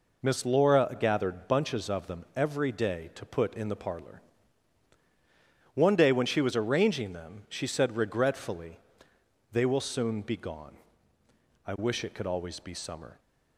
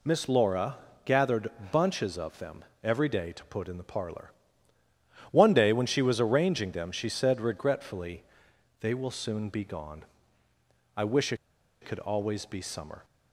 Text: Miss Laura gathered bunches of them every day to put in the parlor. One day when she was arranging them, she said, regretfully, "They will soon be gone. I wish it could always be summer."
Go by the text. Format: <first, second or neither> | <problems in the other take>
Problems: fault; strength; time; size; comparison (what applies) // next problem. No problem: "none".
first | pauses between "Laura" and "gathered"; slight; at 0.7 s; 0.28 s long // pauses between "gathered" and "bunches"; slight; at 1.5 s; 0.22 s long // pauses between "them" and "every"; slight; at 2.6 s; 0.18 s long // pauses between "wish" and "it"; noticeable; at 11.3 s; 0.47 s long